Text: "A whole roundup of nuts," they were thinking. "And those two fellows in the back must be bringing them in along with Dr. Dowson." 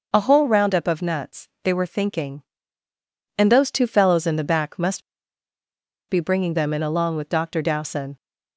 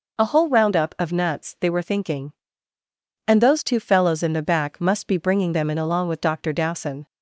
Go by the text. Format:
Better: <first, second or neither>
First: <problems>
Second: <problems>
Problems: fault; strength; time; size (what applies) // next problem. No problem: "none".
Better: second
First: pauses between "must" and "be"; at 5.0 s; 1.0 s long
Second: none